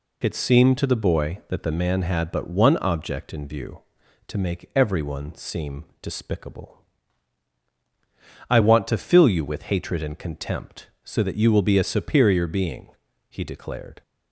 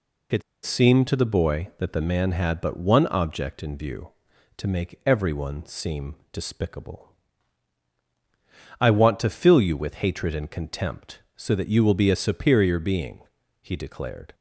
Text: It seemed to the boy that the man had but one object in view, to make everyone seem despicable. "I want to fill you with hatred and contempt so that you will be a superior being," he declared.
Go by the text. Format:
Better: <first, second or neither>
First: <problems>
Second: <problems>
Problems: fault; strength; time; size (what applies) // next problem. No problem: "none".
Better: first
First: pauses between "seem" and "despicable"; slight; at 5.8 s; 0.20 s long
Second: pauses between "It" and "seemed"; slight; at 0.4 s; 0.23 s long // pauses between "seem" and "despicable"; slight; at 6.1 s; 0.20 s long